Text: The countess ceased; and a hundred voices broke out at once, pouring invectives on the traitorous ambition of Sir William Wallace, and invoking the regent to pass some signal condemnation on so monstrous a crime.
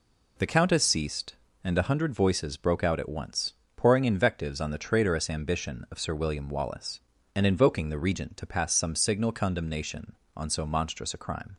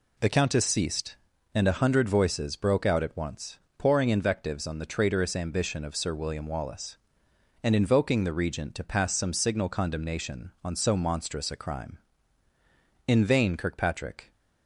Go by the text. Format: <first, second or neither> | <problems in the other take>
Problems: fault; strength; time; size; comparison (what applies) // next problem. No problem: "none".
first | goes on to say "In vain Kirkpatrick"; noticeable; from 13.0 s on; 1.2 s long